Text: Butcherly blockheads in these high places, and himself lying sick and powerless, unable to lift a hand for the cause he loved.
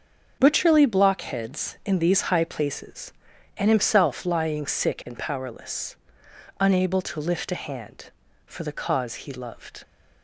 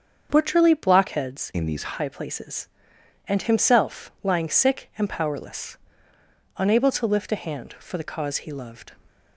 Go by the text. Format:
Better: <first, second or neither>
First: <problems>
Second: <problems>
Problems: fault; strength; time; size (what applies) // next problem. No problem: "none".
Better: first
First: starts louder than the rest; until 1.4 s; 6.5 dB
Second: starts louder than the rest; strong; until 1.3 s; 7 dB // changes voice from "in" to "these"; from 1.5 to 1.9 s; 0.4 s long